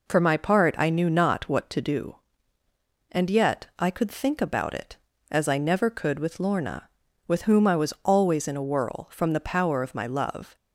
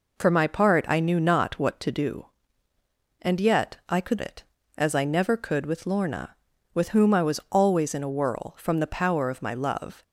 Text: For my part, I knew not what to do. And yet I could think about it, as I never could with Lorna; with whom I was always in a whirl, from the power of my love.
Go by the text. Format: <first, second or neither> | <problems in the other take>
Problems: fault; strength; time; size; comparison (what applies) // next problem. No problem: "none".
first | skips "think about"; at 4.2 s